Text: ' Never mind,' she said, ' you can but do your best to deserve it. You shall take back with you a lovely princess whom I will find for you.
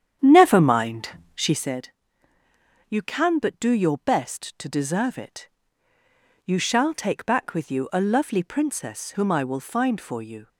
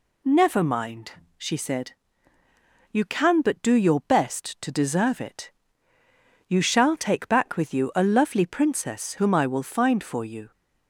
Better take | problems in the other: second | starts louder than the rest; strong; until 1.7 s; 8.5 dB

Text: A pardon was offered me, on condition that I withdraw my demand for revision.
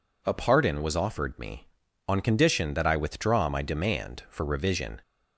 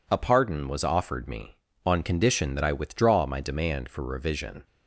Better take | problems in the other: neither | none

